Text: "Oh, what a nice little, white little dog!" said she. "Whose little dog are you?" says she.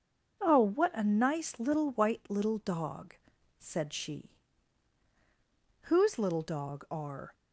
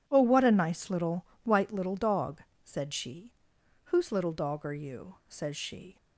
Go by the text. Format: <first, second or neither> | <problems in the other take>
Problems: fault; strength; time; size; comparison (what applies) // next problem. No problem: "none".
second | stops before "you says she"; at 7.3 s